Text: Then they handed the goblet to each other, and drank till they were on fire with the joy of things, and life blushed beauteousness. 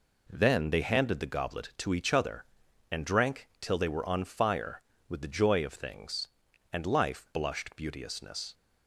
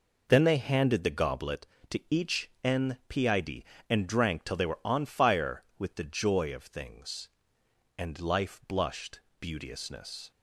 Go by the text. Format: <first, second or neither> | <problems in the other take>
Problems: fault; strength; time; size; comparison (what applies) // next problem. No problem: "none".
first | says "npid" for "other"; at 2.6 s // pauses between "blushed" and "beauteousness"; slight; at 9.2 s; 0.20 s long